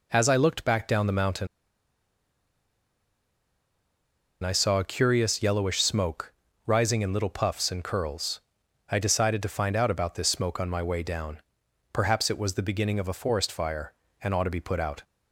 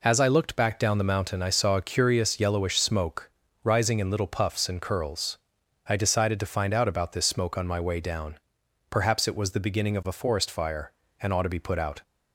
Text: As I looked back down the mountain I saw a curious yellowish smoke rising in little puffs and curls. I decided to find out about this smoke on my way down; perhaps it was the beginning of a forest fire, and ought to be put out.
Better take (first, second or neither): second